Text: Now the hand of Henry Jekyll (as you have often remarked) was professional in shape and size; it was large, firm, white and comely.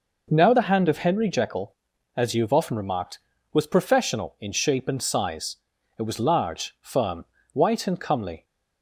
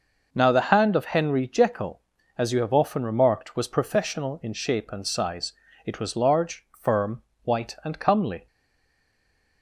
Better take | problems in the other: first | stays silent after the last word; noticeable; from 8.4 s on; 1.2 s long

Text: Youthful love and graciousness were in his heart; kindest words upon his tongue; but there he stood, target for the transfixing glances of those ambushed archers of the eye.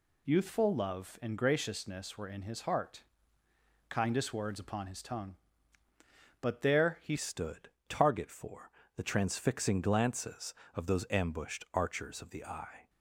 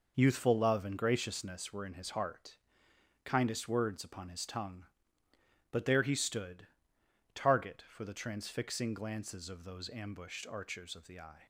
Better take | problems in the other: second | changes voice at "stood"; from 7.1 s on; 5.7 s long // pauses between "for" and "the"; slight; at 8.6 s; 0.28 s long

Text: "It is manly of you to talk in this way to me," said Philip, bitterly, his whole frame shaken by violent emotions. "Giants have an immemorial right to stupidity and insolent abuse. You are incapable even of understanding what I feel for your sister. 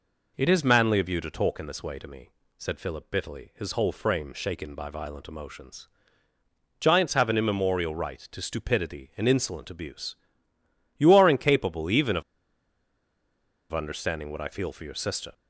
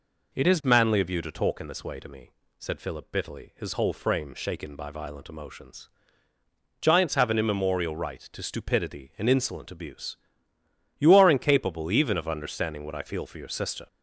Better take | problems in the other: second | pauses between "of" and "understanding"; strong; at 12.2 s; 1.5 s long

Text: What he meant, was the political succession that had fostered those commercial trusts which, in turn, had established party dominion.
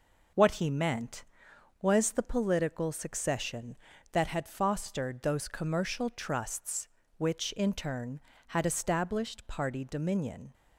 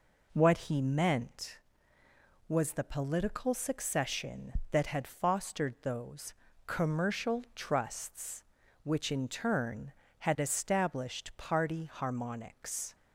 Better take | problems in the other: first | pauses between "those" and "commercial"; slight; at 6.3 s; 0.32 s long // says "harmonics" for "dominion"; at 11.8 s

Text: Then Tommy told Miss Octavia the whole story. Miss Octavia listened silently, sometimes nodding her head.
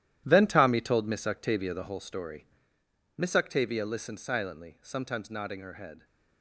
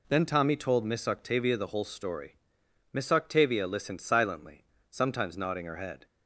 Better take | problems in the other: second | gets quieter; strong; throughout; 11.5 dB

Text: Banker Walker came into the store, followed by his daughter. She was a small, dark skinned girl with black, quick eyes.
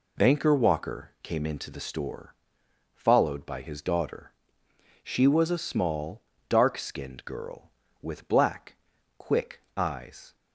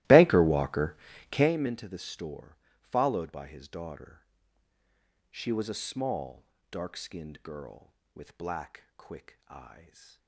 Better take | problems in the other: first | starts louder than the rest; strong; until 1.5 s; 17 dB // pauses between "Walker" and "came"; slight; at 0.9 s; 0.36 s long

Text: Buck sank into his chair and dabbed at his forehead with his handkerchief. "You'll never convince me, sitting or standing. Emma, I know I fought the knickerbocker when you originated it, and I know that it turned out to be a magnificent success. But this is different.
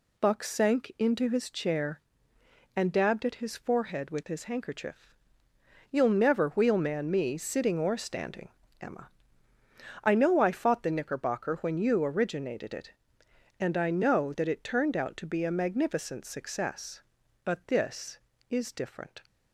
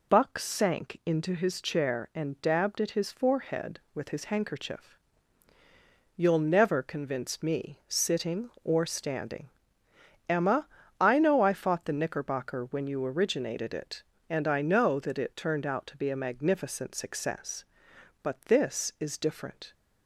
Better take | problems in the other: second | says "wheelman" for "convince"; at 6.5 s

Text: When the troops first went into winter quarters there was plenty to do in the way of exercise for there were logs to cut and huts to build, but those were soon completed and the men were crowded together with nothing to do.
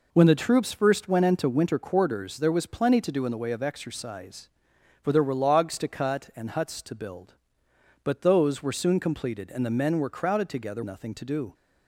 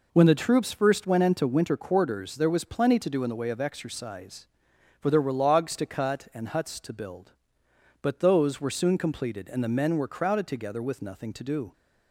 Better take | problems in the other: second | skips "with"; at 10.8 s

